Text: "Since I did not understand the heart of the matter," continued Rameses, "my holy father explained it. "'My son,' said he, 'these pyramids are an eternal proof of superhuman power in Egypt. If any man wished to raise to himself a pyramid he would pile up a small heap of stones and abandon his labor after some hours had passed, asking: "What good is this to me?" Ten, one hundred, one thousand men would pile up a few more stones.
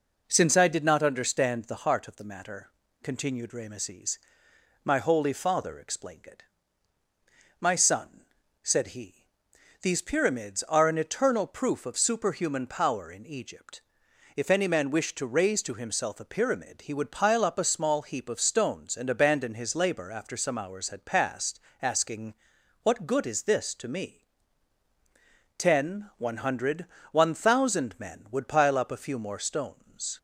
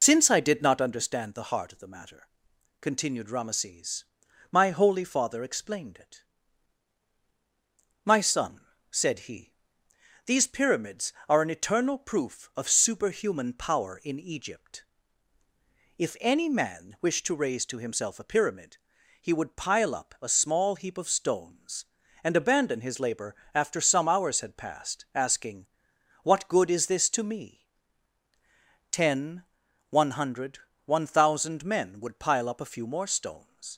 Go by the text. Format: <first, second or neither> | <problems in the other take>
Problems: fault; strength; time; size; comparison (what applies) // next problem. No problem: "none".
first | loses the start of "Since"; at 0.0 s; 60 ms // pauses between "pyramid" and "he"; at 18.7 s; 0.42 s long // pauses between "labor" and "after"; slight; at 23.3 s; 0.20 s long